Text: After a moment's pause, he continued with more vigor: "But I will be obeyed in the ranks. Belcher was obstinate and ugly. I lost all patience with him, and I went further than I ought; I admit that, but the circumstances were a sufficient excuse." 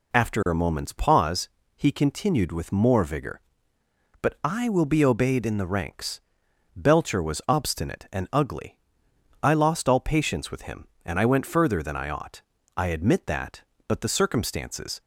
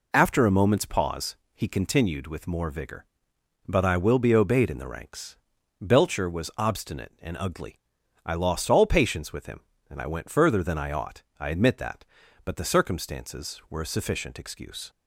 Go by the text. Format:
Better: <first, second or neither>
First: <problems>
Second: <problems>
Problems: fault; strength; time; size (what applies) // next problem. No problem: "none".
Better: second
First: stops before "were a sufficient excuse"; at 15.0 s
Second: none